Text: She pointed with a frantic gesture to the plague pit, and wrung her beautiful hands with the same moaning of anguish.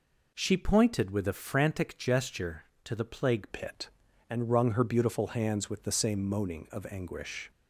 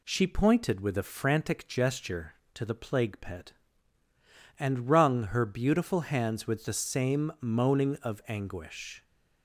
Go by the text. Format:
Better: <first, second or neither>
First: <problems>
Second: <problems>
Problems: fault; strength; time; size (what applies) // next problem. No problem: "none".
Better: second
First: changes voice at "pit"; from 3.5 s on; 4.0 s long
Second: none